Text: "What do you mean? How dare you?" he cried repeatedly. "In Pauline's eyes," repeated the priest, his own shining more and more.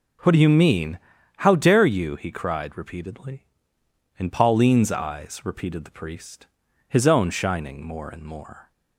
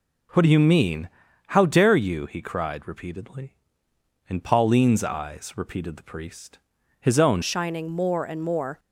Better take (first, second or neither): first